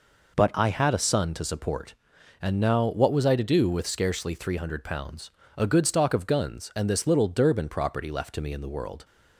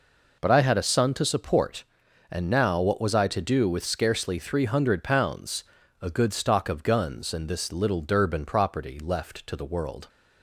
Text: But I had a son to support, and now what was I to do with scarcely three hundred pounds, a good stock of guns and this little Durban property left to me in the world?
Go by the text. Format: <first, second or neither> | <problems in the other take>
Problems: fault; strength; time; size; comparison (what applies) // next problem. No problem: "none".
first | skips "me in"; at 9.5 s